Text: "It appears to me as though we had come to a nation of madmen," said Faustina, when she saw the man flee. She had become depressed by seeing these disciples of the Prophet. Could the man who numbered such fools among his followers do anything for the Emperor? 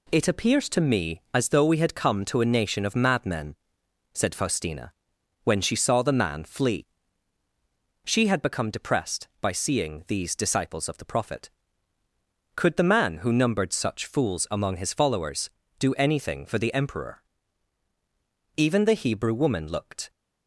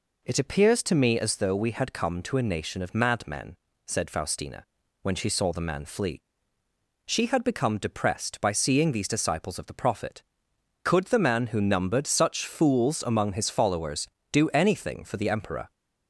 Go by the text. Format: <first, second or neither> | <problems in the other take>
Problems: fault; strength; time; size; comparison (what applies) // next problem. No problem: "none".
second | goes on to say "Even the Hebrew woman looked"; from 18.5 s on; 1.5 s long